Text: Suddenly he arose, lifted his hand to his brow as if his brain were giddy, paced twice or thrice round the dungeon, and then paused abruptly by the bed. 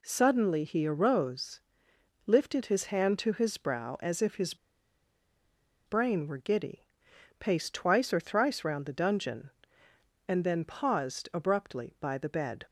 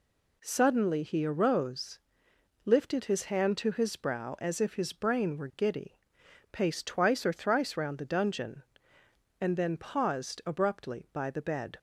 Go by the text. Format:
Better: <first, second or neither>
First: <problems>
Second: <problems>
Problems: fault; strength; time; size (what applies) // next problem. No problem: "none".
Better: second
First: pauses between "his" and "brain"; strong; at 4.5 s; 1.3 s long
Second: none